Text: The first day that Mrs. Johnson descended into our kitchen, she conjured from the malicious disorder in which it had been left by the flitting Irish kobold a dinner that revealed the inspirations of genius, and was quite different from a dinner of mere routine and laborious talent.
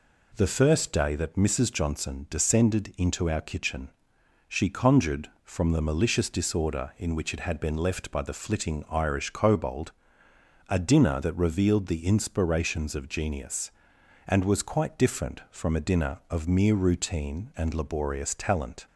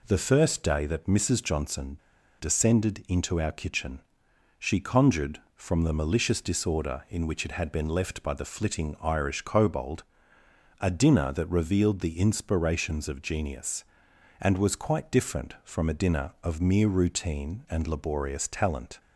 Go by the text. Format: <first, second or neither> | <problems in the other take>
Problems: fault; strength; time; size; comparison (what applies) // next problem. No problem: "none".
first | pauses between "Johnson" and "descended"; at 1.9 s; 0.43 s long // pauses between "kobold" and "a"; noticeable; at 10.0 s; 0.78 s long; noticeable in the first